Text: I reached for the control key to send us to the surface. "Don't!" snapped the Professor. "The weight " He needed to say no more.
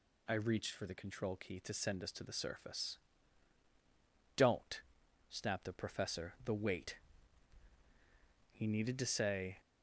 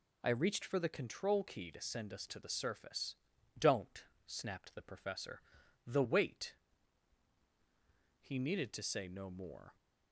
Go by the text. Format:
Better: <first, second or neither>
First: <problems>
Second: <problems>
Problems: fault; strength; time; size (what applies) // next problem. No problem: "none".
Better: second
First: stops before "no more"; at 9.5 s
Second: none